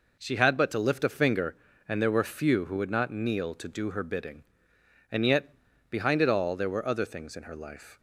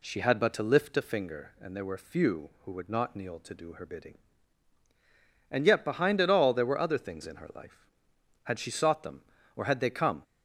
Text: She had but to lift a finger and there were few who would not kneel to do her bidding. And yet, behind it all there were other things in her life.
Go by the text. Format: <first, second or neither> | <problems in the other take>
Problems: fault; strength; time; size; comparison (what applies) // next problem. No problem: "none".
first | goes on to say "Had she sought them or had they come"; strong; from 8.4 s on; 1.7 s long